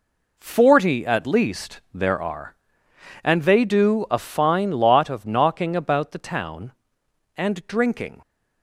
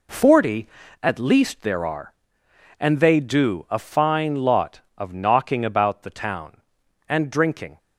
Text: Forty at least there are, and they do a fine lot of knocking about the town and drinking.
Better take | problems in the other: neither | none

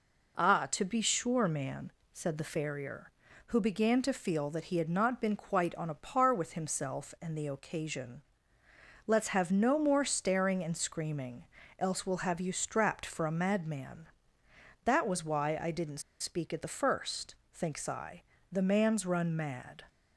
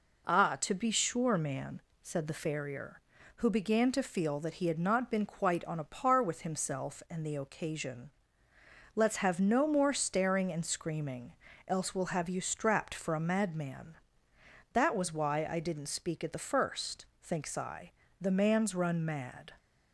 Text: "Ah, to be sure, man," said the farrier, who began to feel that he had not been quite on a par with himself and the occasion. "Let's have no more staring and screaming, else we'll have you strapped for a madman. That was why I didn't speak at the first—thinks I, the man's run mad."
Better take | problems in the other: second | pauses between "didn't" and "speak"; slight; at 16.0 s; 0.19 s long

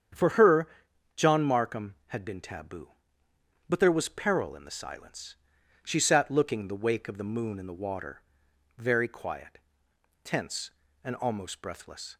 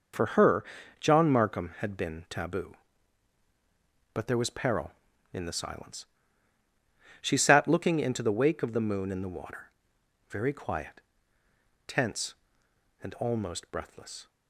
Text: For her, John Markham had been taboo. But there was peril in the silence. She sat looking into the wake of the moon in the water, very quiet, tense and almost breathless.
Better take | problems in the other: second | starts louder than the rest; strong; until 1.6 s; 8 dB // skips "into"; at 6.6 s

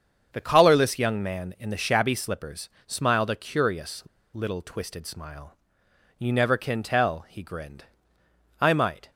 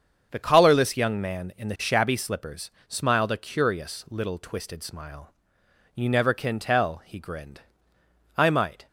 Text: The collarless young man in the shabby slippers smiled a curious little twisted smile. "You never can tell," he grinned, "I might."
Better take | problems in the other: second | starts louder than the rest; until 1.3 s; 7 dB; also in the second // pauses between "slippers" and "smiled"; slight; at 2.6 s; 0.18 s long; slight in the second // pauses between "curious" and "little"; slight; at 4.0 s; 0.32 s long

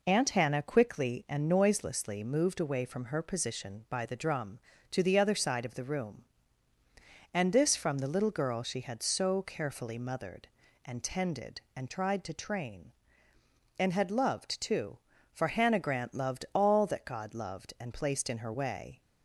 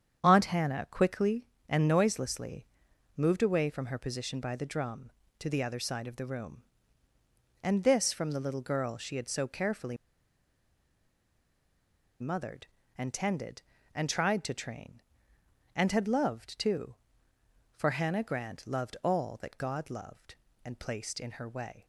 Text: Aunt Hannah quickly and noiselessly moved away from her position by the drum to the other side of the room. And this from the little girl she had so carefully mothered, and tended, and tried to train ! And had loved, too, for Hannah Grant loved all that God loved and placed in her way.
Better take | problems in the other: first | starts louder than the rest; strong; until 1.2 s; 8.5 dB // pauses between "noiselessly" and "moved"; noticeable; at 2.6 s; 0.50 s long // pauses between "carefully" and "mothered"; strong; at 9.9 s; 2.2 s long

